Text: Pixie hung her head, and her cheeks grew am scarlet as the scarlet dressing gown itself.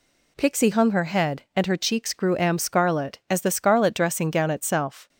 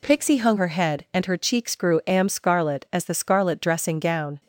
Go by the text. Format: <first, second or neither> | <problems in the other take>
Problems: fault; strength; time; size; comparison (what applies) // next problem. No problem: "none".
first | stops before "itself"; at 4.4 s